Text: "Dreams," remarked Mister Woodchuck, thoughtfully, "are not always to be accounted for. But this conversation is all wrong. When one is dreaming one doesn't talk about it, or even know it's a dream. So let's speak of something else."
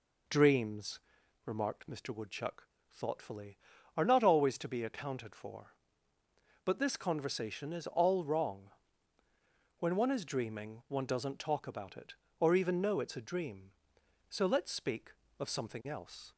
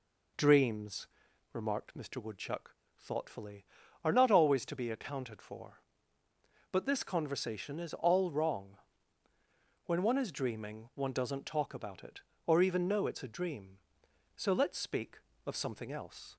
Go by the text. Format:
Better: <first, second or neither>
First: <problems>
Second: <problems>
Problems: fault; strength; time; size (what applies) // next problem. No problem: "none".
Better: neither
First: none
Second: none